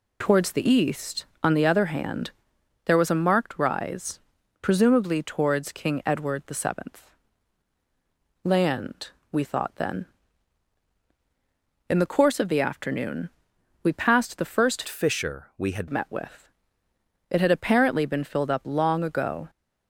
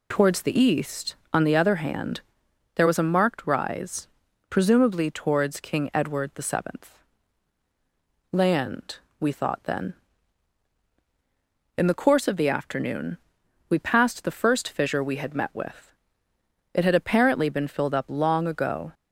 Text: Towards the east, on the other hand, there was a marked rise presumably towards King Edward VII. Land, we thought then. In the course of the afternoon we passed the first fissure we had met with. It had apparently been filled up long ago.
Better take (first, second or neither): second